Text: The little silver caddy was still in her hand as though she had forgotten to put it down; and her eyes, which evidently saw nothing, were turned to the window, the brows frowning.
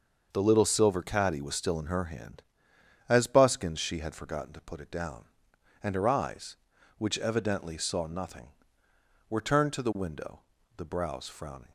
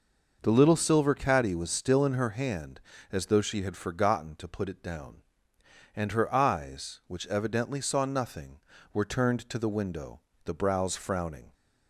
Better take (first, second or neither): second